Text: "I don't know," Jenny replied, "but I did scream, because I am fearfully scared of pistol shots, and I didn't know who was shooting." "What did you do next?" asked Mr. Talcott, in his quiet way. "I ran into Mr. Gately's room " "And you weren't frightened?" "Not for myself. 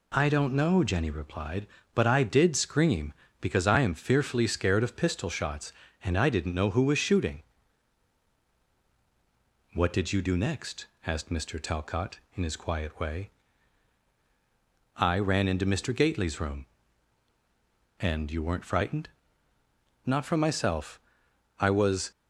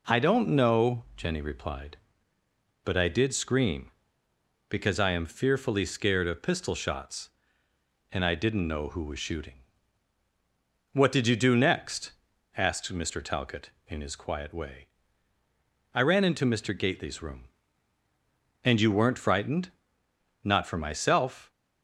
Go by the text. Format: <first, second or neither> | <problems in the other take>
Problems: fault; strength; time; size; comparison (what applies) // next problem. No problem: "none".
second | goes on to say "I was"; from 21.5 s on; 0.52 s long